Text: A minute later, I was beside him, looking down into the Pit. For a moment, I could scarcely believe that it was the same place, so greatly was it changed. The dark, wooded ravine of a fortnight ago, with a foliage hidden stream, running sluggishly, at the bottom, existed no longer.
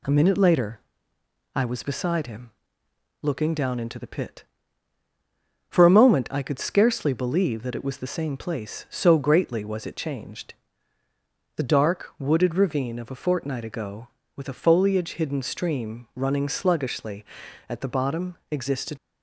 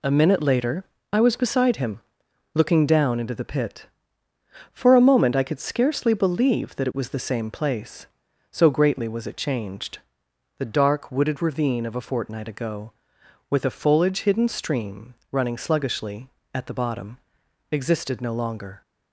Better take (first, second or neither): second